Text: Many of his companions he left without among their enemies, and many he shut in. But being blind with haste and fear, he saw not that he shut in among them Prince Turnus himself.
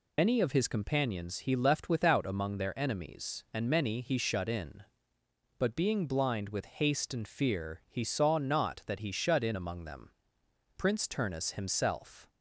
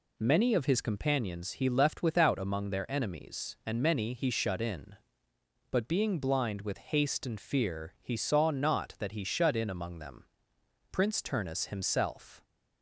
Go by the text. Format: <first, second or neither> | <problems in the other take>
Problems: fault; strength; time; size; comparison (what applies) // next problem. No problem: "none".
second | loses the start of "Many"; at 0.1 s; 130 ms // pauses between "them" and "Prince"; noticeable; at 10.1 s; 0.66 s long; noticeable in the second